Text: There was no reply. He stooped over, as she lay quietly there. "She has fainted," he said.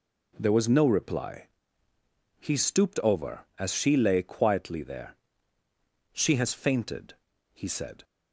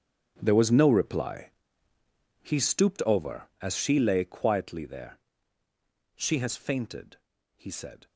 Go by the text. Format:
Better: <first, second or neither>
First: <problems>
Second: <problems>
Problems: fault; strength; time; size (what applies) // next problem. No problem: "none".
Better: first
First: none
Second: gets quieter; strong; throughout; 16.5 dB